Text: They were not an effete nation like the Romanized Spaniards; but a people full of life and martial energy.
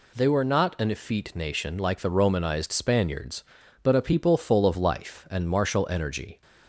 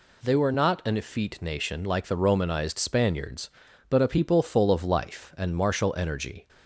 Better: neither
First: none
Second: none

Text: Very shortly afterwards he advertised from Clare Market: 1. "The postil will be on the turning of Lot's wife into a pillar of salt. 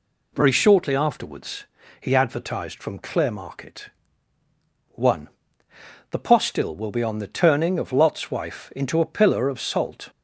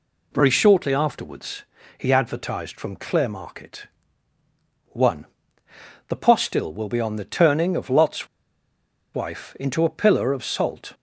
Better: first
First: pauses between "afterwards" and "he"; slight; at 1.6 s; 0.35 s long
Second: pauses between "afterwards" and "he"; slight; at 1.6 s; 0.34 s long // pauses between "Lot's" and "wife"; noticeable; at 8.2 s; 0.88 s long

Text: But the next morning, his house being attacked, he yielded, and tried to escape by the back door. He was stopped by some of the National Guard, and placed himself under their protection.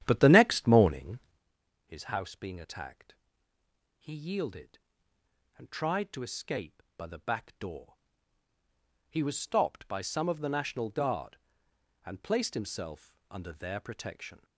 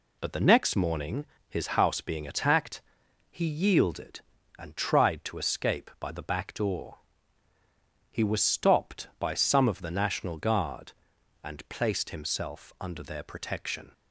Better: second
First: starts louder than the rest; strong; until 1.5 s; 11 dB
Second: none

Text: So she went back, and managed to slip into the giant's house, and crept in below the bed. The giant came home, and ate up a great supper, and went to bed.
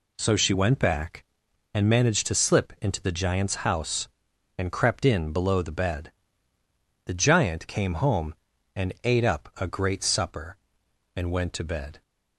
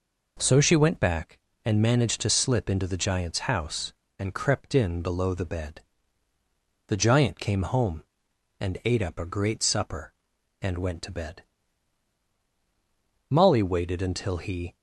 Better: first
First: none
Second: goes on to say "Molly waited until he"; from 13.2 s on; 1.4 s long

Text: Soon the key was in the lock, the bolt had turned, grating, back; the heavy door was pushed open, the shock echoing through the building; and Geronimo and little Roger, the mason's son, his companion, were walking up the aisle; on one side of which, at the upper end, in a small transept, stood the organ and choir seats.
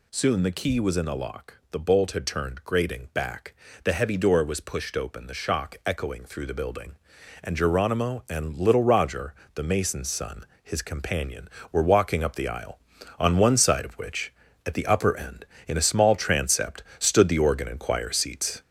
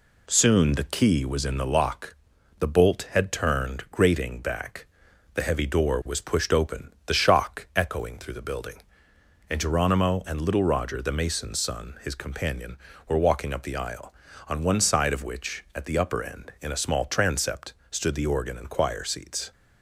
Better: second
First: gets louder; noticeable; throughout; 4.5 dB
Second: none

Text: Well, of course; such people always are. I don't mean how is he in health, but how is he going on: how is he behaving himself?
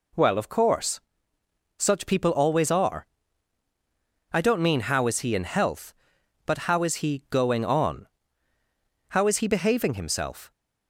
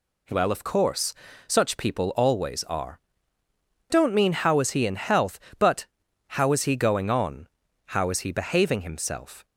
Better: first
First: none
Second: skips "I"; at 3.4 s // pauses between "but" and "how"; noticeable; at 5.8 s; 0.50 s long

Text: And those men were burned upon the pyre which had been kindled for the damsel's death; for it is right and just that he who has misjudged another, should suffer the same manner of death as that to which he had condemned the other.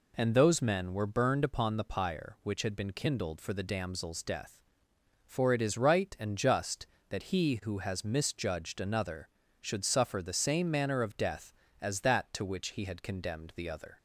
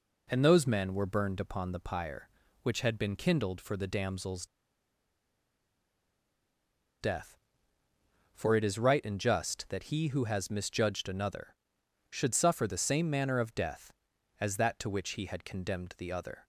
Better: first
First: none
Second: pauses between "damsel's" and "death"; strong; at 4.4 s; 2.5 s long

